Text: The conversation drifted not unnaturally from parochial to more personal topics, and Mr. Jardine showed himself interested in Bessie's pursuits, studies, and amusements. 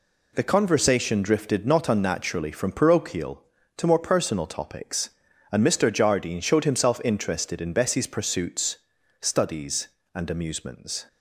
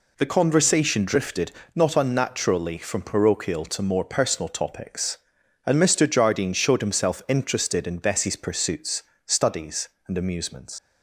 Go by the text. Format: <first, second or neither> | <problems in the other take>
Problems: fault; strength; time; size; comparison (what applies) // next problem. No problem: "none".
first | pauses between "drifted" and "not"; slight; at 1.5 s; 0.24 s long // leaves "amusements" unfinished; at 10.7 s; 80 ms